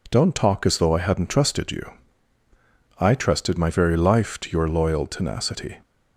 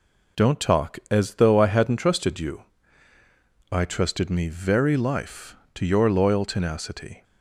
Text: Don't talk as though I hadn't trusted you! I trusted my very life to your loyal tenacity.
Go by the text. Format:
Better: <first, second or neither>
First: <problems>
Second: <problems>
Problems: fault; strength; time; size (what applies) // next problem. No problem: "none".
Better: first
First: none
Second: says "me" for "my"; at 4.2 s